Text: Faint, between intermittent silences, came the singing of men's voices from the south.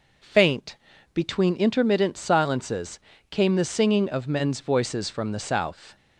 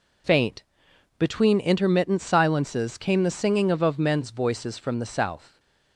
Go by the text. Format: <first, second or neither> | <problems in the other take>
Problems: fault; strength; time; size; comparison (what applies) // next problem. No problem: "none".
first | says "of" twice; at 3.8 s